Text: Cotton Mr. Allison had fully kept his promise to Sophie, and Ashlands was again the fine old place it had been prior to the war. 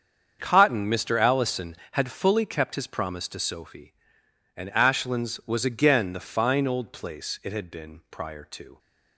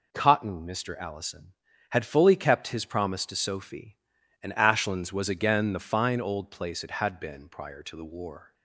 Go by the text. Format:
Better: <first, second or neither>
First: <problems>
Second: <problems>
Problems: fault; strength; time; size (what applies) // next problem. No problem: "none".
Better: second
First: starts louder than the rest; strong; until 1.4 s; 7 dB // stops before "the war"; at 8.7 s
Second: none